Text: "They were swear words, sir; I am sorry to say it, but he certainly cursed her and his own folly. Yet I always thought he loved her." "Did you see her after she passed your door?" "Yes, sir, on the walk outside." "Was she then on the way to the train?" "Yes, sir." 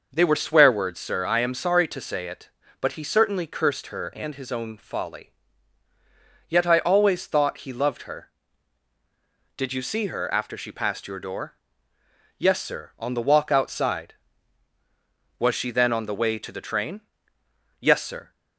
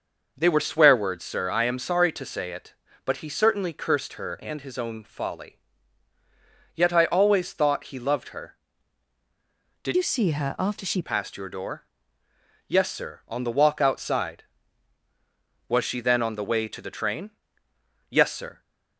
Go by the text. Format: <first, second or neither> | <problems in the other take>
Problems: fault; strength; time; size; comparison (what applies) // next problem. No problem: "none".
first | changes voice from "you" to "she"; from 9.9 to 11.0 s; 1.1 s long